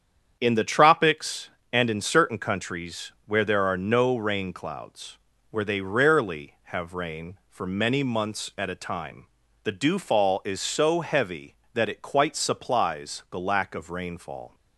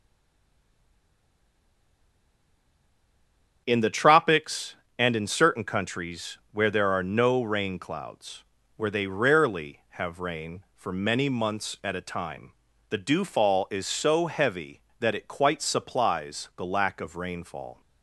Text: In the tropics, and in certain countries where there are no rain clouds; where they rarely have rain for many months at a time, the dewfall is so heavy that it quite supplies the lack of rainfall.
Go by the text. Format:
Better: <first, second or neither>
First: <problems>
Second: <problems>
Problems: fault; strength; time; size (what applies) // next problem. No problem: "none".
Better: first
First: starts louder than the rest; strong; until 1.4 s; 8.5 dB // pauses between "countries" and "where"; slight; at 3.1 s; 0.16 s long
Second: stays silent before the first word; strong; until 3.6 s; 3.6 s long // starts louder than the rest; strong; until 4.6 s; 8 dB // pauses between "countries" and "where"; slight; at 6.3 s; 0.16 s long